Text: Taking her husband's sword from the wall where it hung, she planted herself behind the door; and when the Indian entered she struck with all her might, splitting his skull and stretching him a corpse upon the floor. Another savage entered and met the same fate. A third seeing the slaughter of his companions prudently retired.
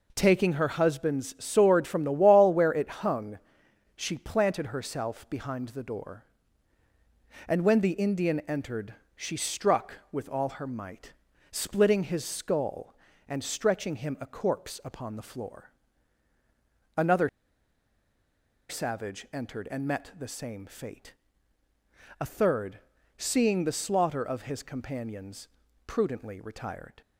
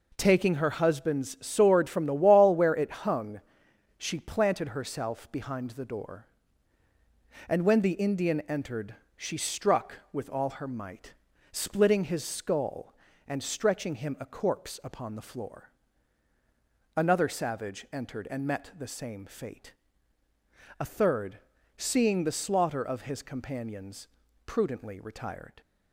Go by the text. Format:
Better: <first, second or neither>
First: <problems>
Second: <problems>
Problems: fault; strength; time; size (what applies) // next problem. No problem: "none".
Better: second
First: pauses between "entered" and "she"; slight; at 8.9 s; 0.20 s long // pauses between "Another" and "savage"; strong; at 17.2 s; 1.4 s long // pauses between "third" and "seeing"; at 22.7 s; 0.38 s long // pauses between "companions" and "prudently"; at 25.4 s; 0.38 s long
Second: pauses between "entered" and "she"; slight; at 8.9 s; 0.20 s long // pauses between "third" and "seeing"; at 21.3 s; 0.38 s long // pauses between "companions" and "prudently"; at 24.0 s; 0.38 s long